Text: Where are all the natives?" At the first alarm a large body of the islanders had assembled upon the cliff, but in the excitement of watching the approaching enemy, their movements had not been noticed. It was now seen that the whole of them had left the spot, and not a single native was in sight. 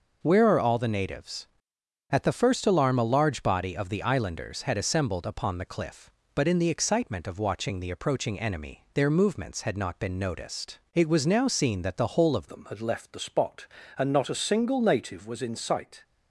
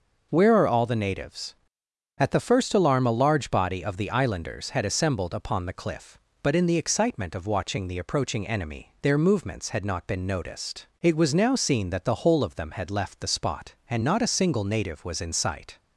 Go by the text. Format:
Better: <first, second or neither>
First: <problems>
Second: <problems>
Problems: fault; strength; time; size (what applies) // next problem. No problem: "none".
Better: second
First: changes voice at "them"; from 12.4 s on; 3.6 s long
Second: none